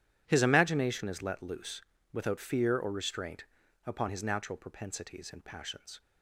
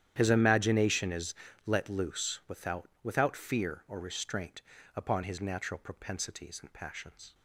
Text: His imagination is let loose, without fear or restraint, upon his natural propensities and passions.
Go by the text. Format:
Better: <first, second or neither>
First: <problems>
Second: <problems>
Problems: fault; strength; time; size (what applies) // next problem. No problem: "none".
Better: first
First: starts louder than the rest; strong; until 1.2 s; 10.5 dB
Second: starts louder than the rest; strong; until 1.1 s; 10.5 dB // pauses between "is" and "let"; slight; at 1.3 s; 0.32 s long // says "without" twice; at 3.0 s